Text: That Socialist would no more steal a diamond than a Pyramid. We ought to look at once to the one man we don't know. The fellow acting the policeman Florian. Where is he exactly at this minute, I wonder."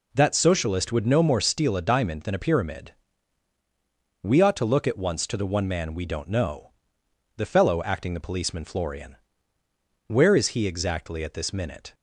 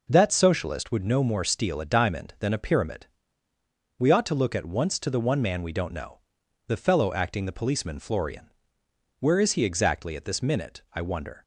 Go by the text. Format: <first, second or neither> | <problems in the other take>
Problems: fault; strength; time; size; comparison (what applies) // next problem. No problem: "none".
second | stops before "I wonder"; at 11.9 s